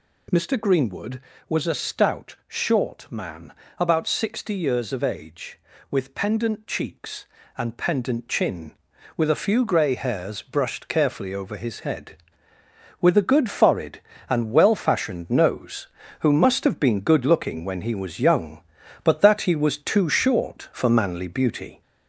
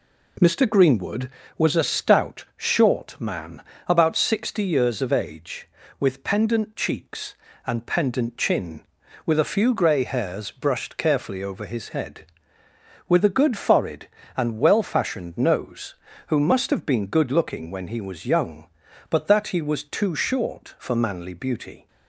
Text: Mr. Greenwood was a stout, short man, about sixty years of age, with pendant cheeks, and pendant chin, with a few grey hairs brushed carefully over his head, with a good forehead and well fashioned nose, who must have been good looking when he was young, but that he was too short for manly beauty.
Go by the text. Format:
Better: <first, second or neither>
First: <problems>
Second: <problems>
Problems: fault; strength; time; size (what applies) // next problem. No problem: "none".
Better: second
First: gets louder; throughout; 4 dB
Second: none